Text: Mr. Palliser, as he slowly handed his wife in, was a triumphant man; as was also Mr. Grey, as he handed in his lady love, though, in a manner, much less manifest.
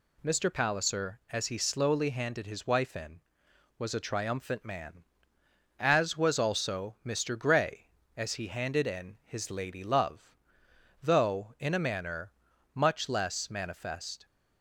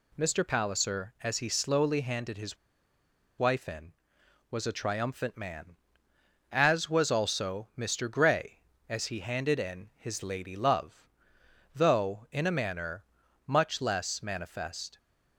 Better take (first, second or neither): first